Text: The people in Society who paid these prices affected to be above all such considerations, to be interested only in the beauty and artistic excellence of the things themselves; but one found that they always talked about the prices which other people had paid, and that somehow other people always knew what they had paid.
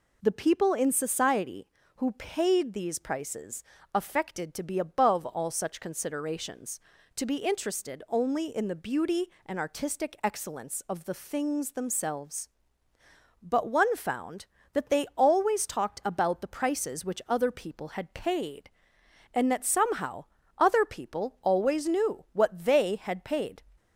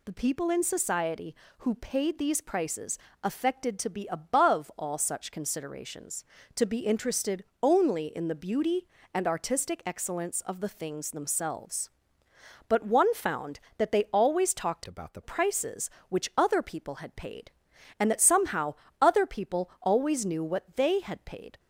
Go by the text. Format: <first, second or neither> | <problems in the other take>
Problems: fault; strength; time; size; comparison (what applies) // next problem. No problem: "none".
first | pauses between "prices" and "affected"; slight; at 2.9 s; 0.26 s long; slight in the first // pauses between "interested" and "only"; slight; at 7.4 s; 0.18 s long // changes voice from "about" to "the"; from 14.8 to 15.2 s; 0.4 s long // pauses between "somehow" and "other"; slight; at 18.7 s; 0.26 s long; slight in the first